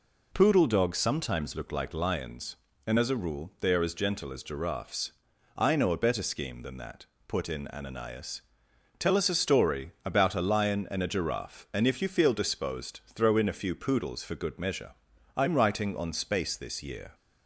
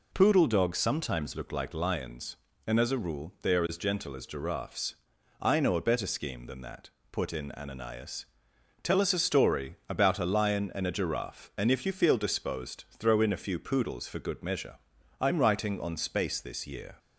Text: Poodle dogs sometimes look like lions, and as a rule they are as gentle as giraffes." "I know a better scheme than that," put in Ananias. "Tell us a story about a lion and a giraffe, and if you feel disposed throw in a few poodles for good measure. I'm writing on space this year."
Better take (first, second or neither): neither